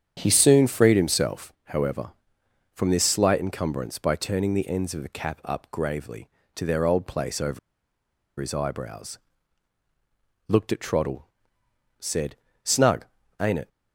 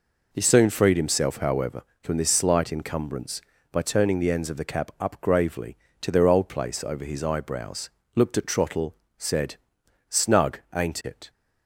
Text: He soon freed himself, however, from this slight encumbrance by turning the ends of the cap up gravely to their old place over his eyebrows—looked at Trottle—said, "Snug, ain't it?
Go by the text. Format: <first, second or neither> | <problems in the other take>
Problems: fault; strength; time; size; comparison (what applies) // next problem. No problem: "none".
second | starts louder than the rest; strong; until 1.1 s; 8.5 dB // pauses between "over" and "his"; noticeable; at 7.5 s; 0.80 s long